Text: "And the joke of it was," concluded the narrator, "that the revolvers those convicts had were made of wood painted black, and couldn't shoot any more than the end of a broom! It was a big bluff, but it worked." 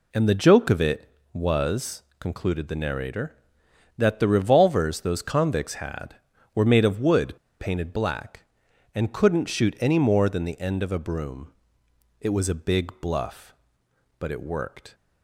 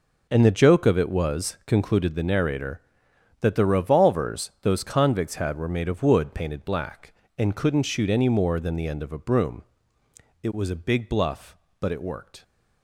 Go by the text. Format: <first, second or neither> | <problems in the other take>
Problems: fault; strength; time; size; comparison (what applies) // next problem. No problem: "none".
second | pauses between "wood" and "painted"; slight; at 7.3 s; 0.25 s long